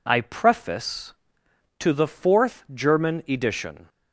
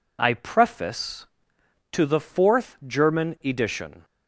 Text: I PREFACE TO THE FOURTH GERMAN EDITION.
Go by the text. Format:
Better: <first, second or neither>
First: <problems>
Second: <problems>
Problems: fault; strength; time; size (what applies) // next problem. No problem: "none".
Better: neither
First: none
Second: none